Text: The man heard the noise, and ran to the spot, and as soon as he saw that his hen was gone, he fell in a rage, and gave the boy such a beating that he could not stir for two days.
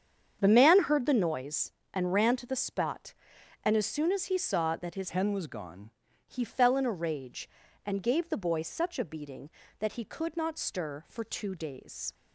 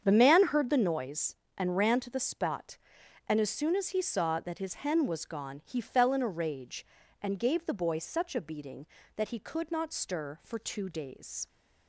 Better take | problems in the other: second | starts louder than the rest; strong; until 1.4 s; 8 dB; strong in the second // changes voice from "hen" to "gone"; from 5.0 to 5.8 s; 0.8 s long

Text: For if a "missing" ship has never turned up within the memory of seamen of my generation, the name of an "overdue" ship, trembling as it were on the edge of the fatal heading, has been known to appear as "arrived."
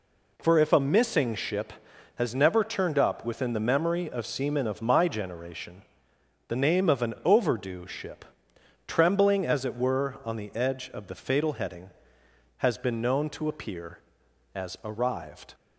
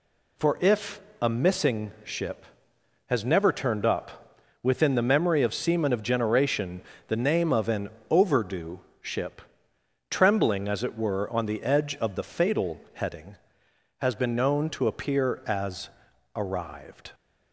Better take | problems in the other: first | pauses between "if" and "a"; slight; at 1.0 s; 0.22 s long // pauses between "up" and "within"; slight; at 4.3 s; 0.26 s long // skips "my"; at 6.0 s // pauses between "an" and "overdue"; slight; at 7.8 s; 0.22 s long // pauses between "overdue" and "ship"; slight; at 8.8 s; 0.20 s long // pauses between "as" and "arrived"; noticeable; at 15.8 s; 0.46 s long

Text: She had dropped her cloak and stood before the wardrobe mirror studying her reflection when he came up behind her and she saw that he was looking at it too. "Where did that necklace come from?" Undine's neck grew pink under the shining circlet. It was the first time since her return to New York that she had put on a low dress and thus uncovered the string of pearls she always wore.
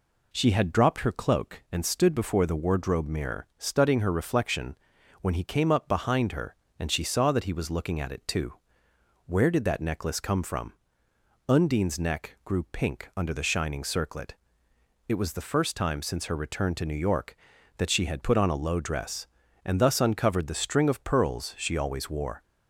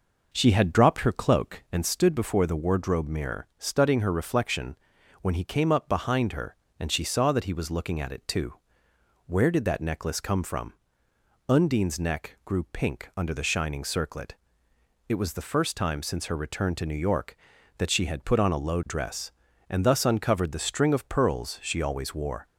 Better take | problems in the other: first | starts louder than the rest; noticeable; until 1.9 s; 5.5 dB // pauses between "reflection" and "when"; at 4.7 s; 0.44 s long; also in the first

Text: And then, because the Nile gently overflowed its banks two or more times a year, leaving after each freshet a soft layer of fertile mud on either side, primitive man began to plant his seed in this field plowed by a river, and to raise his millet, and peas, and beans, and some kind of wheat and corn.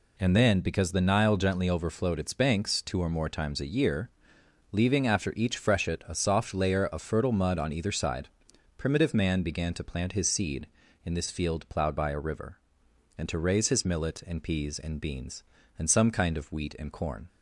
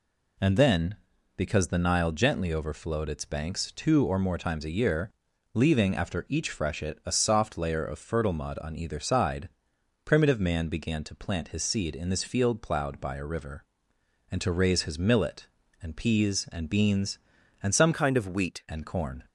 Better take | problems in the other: first | changes voice from "kind" to "wheat"; from 17.9 to 18.6 s; 0.7 s long

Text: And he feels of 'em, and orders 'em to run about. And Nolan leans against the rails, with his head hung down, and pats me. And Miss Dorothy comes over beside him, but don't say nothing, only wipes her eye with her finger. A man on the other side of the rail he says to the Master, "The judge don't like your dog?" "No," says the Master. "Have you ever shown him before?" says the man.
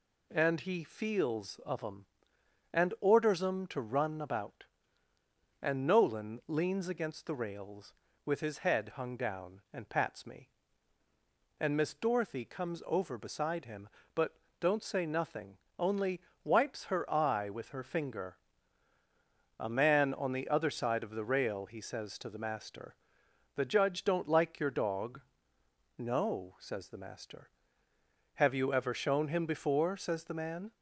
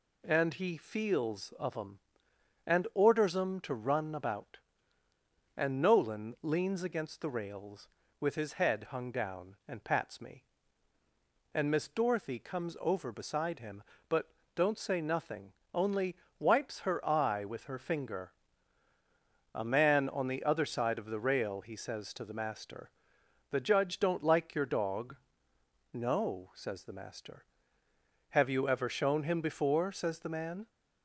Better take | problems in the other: neither | pauses between "but" and "don't"; slight; the same in both // pauses between "only" and "wipes"; slight; the same in both

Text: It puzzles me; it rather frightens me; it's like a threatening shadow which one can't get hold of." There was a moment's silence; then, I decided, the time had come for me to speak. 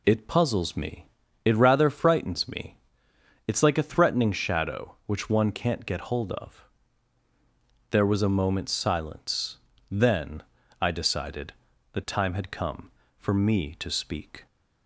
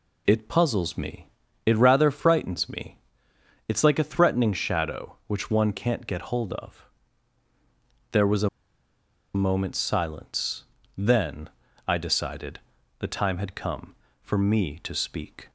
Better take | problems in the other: first | pauses between "a" and "moment's"; noticeable; at 8.4 s; 0.86 s long

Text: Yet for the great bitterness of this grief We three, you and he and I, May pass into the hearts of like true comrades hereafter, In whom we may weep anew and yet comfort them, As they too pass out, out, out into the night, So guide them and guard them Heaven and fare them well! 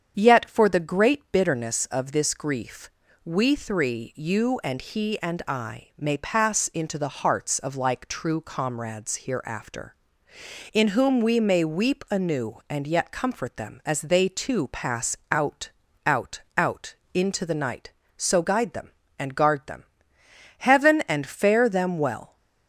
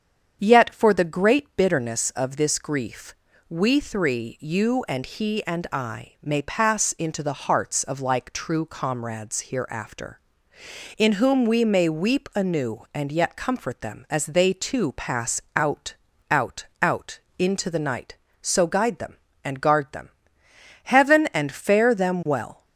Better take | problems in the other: neither | starts louder than the rest; strong; the same in both // pauses between "grief" and "We"; slight; the same in both // pauses between "out" and "into"; slight; the same in both // pauses between "them" and "Heaven"; noticeable; the same in both

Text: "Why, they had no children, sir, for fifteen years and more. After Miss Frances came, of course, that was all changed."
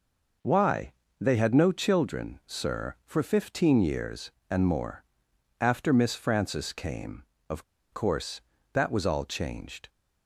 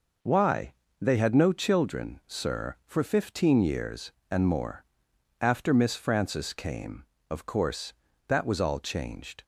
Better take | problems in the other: second | pauses between "of" and "course"; slight; at 7.6 s; 0.30 s long

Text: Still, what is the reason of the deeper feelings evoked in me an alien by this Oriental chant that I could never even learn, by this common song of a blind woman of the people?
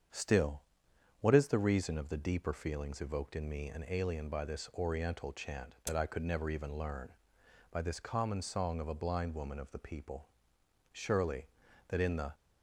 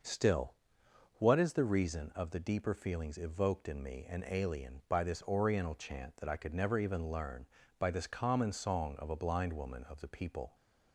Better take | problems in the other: second | starts louder than the rest; strong; until 1.7 s; 7.5 dB; noticeable in the second // goes on to say "Surely that in the"; from 10.9 s on; 1.4 s long

